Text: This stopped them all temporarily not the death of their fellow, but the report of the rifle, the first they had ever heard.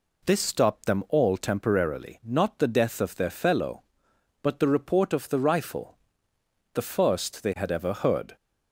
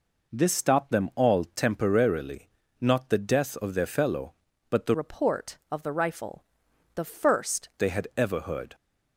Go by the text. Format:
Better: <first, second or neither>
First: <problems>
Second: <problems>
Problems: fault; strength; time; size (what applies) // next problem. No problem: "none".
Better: first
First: none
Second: pauses between "temporarily" and "not"; slight; at 2.4 s; 0.30 s long // changes voice from "report" to "first"; from 4.9 to 7.6 s; 2.7 s long